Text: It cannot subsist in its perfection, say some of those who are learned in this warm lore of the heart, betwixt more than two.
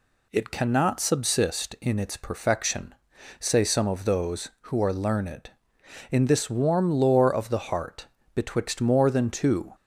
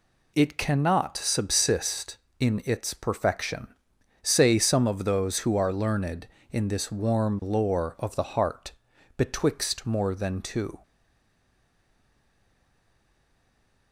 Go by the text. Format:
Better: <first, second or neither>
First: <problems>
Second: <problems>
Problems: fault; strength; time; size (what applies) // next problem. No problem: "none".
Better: first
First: none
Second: stays silent after the last word; strong; from 10.8 s on; 3.1 s long